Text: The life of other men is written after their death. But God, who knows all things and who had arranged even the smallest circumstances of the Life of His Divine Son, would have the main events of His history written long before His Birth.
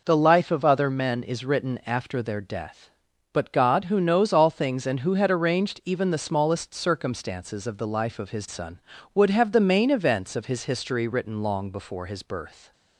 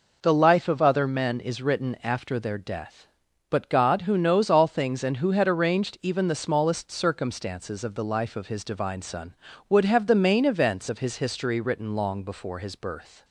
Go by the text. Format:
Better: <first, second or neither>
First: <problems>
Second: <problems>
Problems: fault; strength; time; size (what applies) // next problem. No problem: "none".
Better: second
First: skips "Divine"; at 8.4 s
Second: none